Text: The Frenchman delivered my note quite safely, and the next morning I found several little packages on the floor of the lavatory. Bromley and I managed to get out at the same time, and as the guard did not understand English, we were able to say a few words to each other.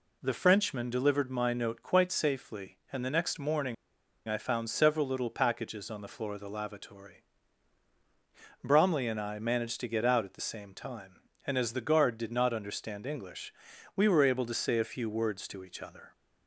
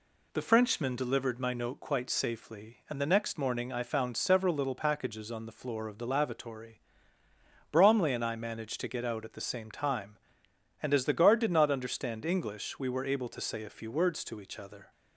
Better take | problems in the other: second | pauses between "morning" and "I"; noticeable; at 3.7 s; 0.53 s long

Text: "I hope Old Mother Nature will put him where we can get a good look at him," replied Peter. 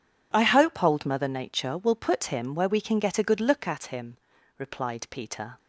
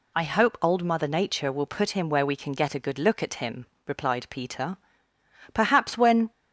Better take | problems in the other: first | goes on to say "Perhaps when"; noticeable; from 5.5 s on; 0.78 s long

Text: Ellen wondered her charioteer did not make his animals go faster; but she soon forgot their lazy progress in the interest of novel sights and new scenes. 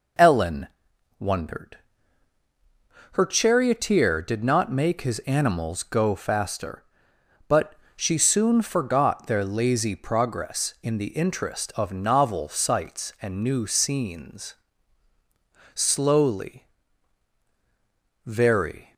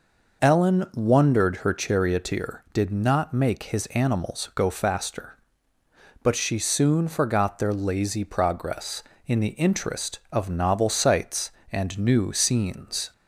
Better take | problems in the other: second | pauses between "Ellen" and "wondered"; noticeable; at 0.6 s; 0.52 s long // pauses between "wondered" and "her"; strong; at 1.7 s; 1.3 s long // pauses between "but" and "she"; slight; at 7.7 s; 0.20 s long // goes on to say "Slowly very"; strong; from 15.7 s on; 3.1 s long

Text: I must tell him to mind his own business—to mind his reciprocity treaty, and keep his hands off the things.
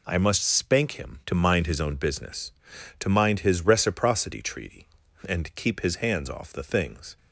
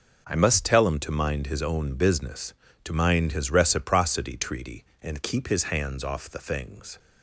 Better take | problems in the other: second | says "spank" for "tell"; at 0.4 s

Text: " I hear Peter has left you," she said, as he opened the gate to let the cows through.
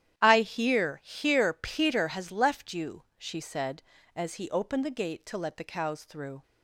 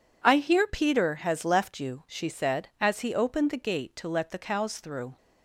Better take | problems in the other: second | starts louder than the rest; strong; until 1.2 s; 11 dB // says "hear" twice; at 1.0 s

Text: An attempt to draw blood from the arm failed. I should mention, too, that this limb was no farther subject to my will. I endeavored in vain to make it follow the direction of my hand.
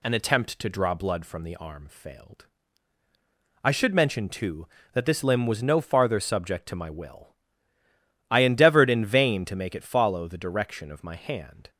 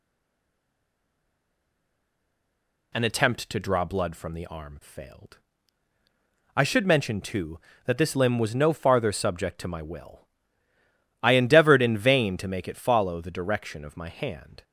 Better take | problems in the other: first | stays silent before the first word; strong; until 2.9 s; 2.9 s long

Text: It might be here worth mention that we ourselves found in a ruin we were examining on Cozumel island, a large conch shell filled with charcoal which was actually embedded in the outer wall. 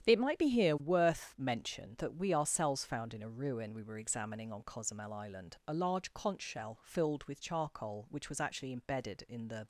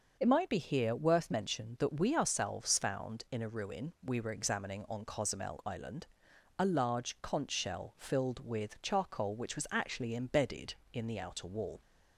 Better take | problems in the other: second | starts louder than the rest; strong; until 1.0 s; 10 dB; noticeable in the second // stops before "outer wall"; at 9.6 s

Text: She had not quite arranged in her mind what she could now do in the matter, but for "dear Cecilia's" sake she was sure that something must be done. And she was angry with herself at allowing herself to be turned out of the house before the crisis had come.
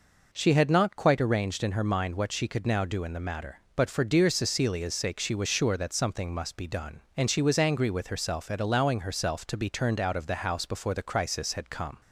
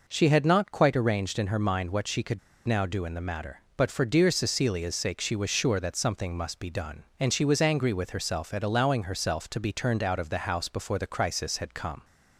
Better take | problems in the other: first | pauses between "could" and "now"; slight; at 2.3 s; 0.26 s long

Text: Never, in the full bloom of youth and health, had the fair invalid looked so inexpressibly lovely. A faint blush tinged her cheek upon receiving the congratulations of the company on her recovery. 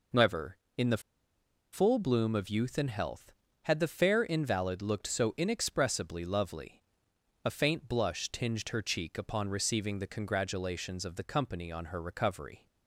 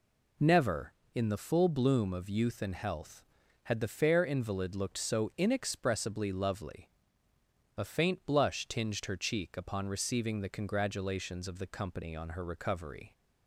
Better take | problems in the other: second | pauses between "the" and "full"; noticeable; at 1.0 s; 0.72 s long

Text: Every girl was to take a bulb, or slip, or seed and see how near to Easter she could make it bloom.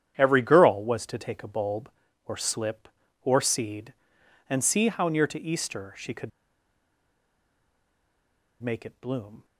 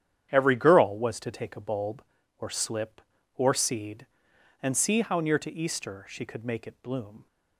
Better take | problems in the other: second | starts louder than the rest; strong; until 1.1 s; 9.5 dB; strong in the second // pauses between "could" and "make"; strong; at 6.3 s; 2.3 s long

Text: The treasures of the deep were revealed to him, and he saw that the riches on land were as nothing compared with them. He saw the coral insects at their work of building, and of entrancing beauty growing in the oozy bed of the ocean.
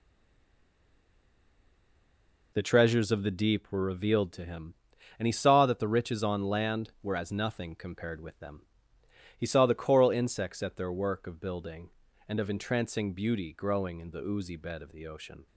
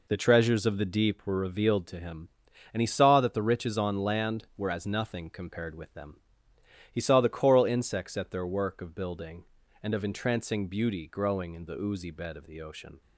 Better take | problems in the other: second | stays silent before the first word; strong; until 2.5 s; 2.5 s long

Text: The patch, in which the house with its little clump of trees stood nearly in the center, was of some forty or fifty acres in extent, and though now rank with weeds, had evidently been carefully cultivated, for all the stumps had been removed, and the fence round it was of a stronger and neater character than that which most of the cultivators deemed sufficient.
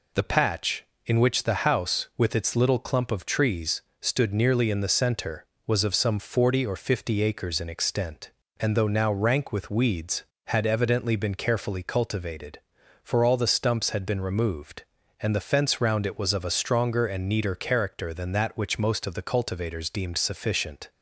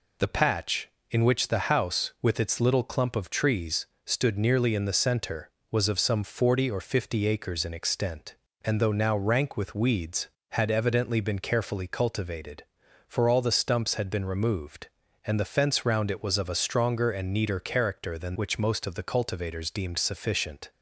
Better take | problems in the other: first | pauses between "trees" and "stood"; slight; at 3.8 s; 0.18 s long; slight in the first // skips "that"; at 18.3 s

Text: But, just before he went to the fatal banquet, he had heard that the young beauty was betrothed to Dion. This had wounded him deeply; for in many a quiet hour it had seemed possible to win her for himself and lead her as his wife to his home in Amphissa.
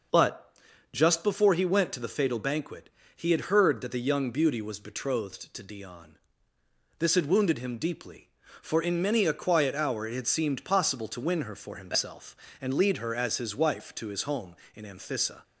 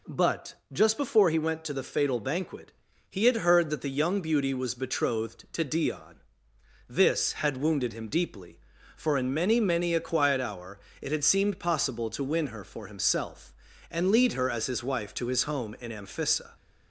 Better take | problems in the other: first | says "many" twice; at 9.6 s // pauses between "hour" and "it"; slight; at 10.7 s; 0.24 s long

